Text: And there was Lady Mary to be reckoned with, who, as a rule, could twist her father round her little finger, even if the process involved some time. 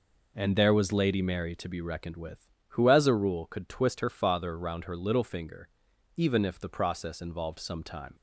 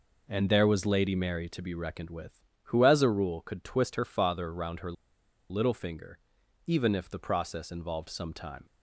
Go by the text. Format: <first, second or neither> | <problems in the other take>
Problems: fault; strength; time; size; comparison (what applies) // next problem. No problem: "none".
first | pauses between "her" and "little"; noticeable; at 4.9 s; 0.57 s long